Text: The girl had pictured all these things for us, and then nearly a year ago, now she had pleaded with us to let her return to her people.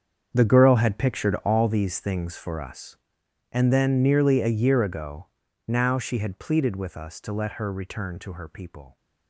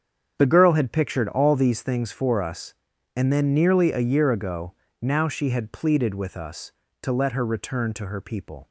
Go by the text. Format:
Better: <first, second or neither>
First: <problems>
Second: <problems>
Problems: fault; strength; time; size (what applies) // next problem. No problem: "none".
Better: second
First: gets quieter; strong; throughout; 14 dB // starts louder than the rest; strong; until 1.3 s; 7 dB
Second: starts louder than the rest; strong; until 1.3 s; 7.5 dB